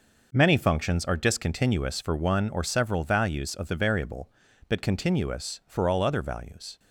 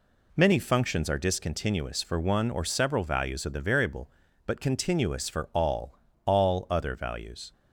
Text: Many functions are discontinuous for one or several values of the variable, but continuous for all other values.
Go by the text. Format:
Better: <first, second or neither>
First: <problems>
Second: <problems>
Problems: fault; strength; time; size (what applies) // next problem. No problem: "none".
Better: first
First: none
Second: says "all" twice; at 6.2 s